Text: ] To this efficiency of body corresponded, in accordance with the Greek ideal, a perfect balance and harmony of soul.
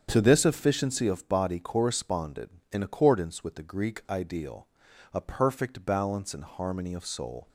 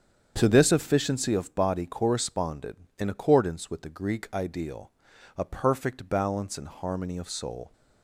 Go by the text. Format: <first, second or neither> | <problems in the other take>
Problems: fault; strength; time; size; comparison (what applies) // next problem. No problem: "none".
neither | starts louder than the rest; strong; the same in both